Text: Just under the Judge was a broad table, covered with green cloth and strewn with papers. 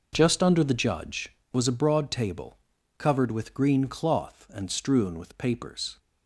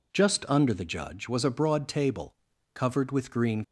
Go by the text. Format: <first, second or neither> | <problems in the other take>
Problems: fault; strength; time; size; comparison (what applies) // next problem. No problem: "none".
first | stops before "cloth and strewn with papers"; at 3.6 s